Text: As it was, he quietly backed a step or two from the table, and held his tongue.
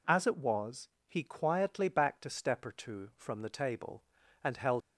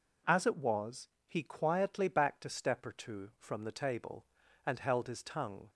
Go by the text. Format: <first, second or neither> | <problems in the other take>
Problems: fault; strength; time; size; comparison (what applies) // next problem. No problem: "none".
second | stops before "his tongue"; at 4.8 s